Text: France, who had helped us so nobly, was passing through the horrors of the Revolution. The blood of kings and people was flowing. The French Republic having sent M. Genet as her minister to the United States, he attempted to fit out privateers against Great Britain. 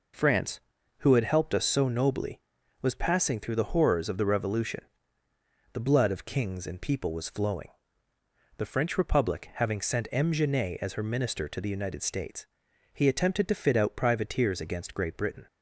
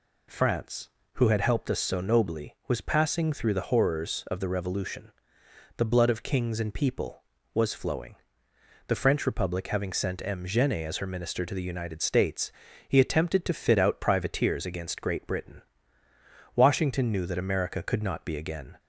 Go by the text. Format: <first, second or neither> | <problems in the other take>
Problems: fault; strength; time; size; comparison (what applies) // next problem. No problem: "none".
first | goes on to say "Washington knew that America could not be again"; strong; from 16.5 s on; 2.2 s long